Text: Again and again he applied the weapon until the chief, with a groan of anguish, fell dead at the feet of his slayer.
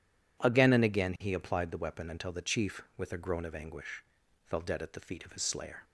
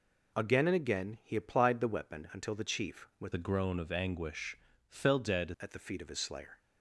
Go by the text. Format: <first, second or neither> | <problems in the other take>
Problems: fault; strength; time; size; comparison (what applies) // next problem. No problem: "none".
first | changes voice from "a" to "dead"; from 3.3 to 5.5 s; 2.2 s long